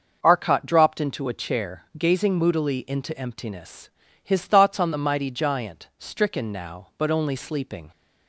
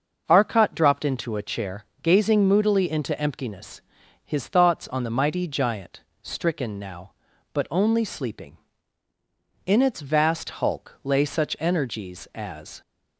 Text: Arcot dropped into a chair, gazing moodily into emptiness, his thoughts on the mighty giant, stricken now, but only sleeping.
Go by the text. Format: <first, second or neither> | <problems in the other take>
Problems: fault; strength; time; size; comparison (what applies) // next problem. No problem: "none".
first | starts louder than the rest; until 1.2 s; 6 dB; noticeable in the first // goes on to say "In its vast hulk lay such energies as"; strong; from 9.6 s on; 3.1 s long